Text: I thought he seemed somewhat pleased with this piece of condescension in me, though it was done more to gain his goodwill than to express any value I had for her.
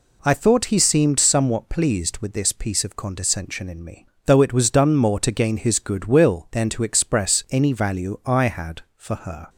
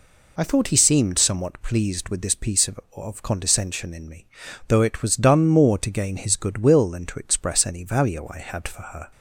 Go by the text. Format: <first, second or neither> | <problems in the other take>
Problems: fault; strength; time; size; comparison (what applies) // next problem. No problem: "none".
first | says "of" twice; at 2.9 s